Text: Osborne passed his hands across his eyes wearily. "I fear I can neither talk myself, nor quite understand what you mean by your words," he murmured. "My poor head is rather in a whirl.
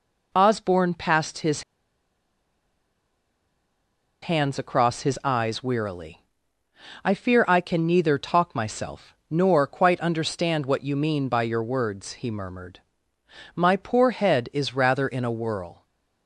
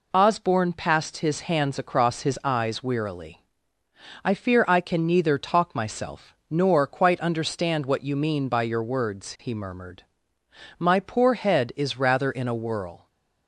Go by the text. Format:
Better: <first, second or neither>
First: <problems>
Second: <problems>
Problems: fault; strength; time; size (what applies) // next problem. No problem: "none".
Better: second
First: pauses between "his" and "hands"; strong; at 1.6 s; 2.6 s long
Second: none